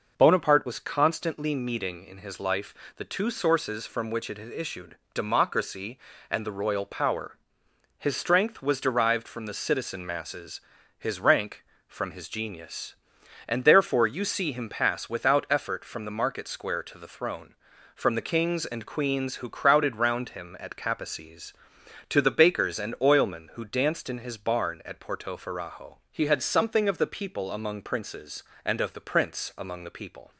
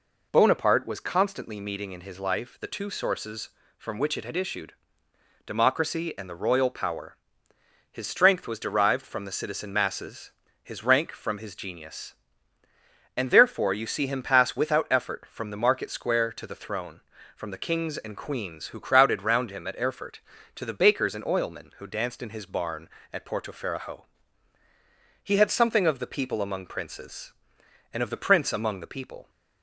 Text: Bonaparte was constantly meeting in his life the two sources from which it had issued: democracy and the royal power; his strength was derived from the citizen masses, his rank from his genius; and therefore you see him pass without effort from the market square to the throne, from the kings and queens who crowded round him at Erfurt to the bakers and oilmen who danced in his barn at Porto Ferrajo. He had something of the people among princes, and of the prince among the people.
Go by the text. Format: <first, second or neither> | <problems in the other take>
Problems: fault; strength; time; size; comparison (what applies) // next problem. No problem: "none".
second | pauses between "life" and "the"; slight; at 2.7 s; 0.22 s long // says "Capaces" for "Erfurt"; at 20.7 s